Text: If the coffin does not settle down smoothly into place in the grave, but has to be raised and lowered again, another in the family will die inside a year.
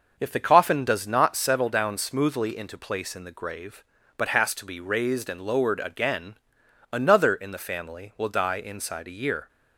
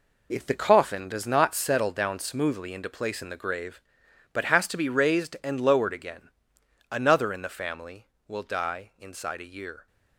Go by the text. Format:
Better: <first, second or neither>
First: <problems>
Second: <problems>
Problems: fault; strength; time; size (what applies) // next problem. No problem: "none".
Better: first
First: none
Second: gets quieter; strong; throughout; 9.5 dB